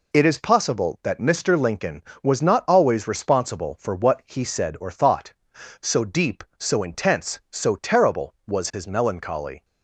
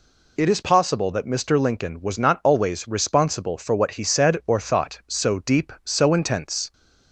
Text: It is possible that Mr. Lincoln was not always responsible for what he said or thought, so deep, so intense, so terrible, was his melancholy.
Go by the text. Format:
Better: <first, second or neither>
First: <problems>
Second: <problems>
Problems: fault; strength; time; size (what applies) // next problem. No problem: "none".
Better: first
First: none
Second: stops before "so terrible was his melancholy"; at 6.7 s